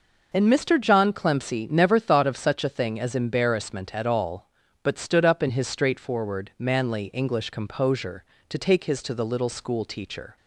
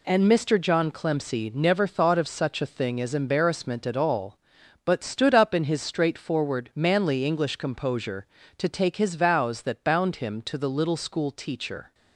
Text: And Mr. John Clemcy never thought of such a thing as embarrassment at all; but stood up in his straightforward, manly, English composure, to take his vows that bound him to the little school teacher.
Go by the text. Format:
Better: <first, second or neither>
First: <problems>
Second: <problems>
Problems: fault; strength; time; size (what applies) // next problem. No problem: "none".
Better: second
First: skips "vows that bound him"; at 9.0 s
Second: none